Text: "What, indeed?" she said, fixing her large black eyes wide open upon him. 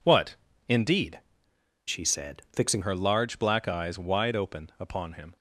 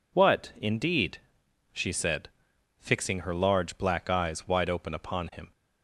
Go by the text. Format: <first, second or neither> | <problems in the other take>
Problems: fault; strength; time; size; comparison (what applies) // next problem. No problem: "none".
second | changes voice from "she" to "fixing"; from 1.8 to 2.8 s; 1.0 s long